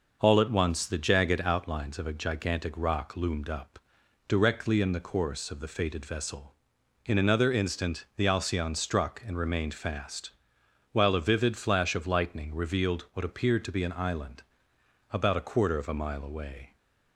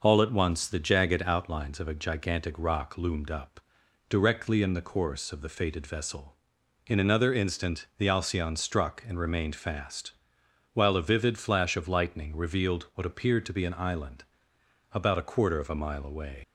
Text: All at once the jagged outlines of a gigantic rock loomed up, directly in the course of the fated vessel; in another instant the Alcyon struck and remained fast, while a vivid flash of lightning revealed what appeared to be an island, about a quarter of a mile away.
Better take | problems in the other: first | leaves "away" unfinished; at 16.4 s; 120 ms

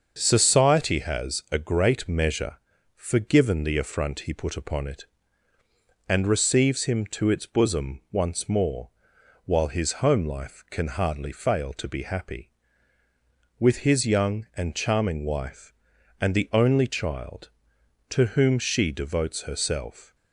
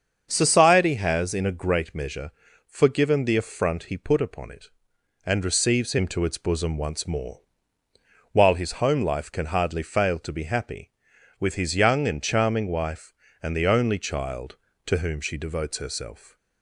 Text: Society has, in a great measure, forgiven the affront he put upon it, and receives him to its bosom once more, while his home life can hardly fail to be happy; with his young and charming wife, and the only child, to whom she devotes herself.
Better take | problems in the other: second | starts louder than the rest; until 1.1 s; 6.5 dB; also in the second // skips "in"; at 1.4 s

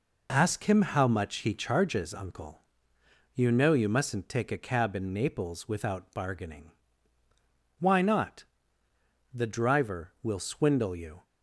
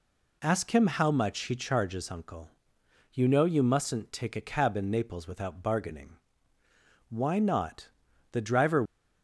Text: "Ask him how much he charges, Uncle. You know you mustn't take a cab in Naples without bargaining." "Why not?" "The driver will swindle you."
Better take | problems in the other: first | stops before "will swindle you"; at 8.8 s

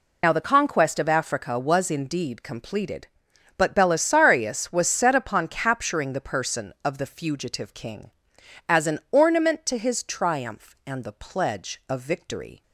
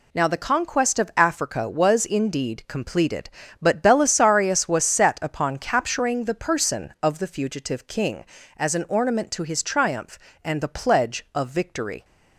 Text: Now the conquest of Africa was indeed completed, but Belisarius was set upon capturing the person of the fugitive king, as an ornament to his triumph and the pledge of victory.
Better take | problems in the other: second | loses the start of "Now"; at 0.2 s; 85 ms

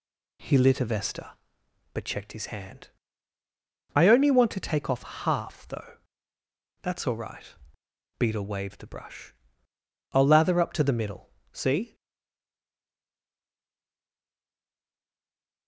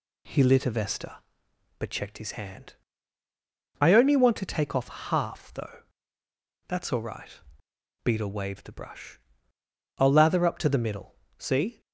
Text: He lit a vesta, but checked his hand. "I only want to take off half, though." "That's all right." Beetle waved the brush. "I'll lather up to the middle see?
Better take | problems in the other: second | pauses between "middle" and "see"; slight; at 11.2 s; 0.24 s long; slight in the second // stays silent after the last word; strong; from 11.9 s on; 3.7 s long

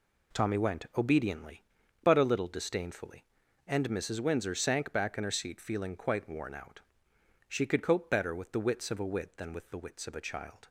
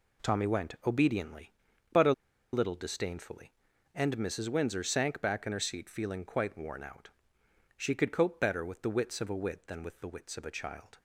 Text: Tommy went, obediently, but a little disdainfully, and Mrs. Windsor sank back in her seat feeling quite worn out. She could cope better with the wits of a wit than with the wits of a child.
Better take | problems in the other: first | pauses between "a" and "little"; at 2.1 s; 0.40 s long

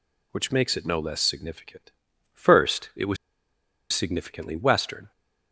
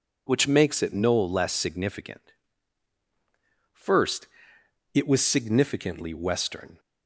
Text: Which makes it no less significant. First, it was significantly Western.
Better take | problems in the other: second | pauses between "was" and "significantly"; noticeable; at 3.1 s; 0.76 s long

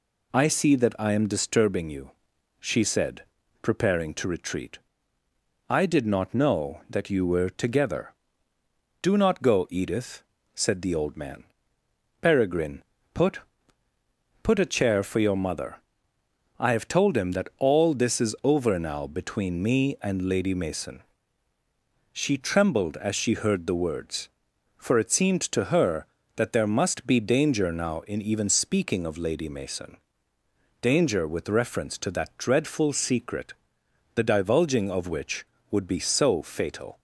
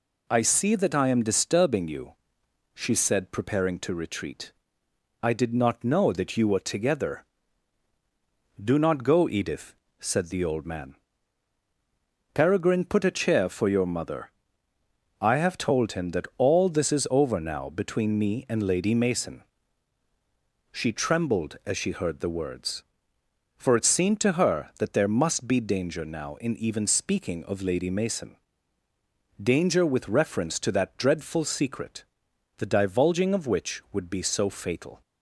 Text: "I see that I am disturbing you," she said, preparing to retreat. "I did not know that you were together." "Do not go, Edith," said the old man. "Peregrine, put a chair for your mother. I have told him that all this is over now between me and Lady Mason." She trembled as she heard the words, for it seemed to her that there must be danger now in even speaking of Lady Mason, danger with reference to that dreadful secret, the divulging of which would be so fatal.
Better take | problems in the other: second | says "put" twice; at 14.4 s

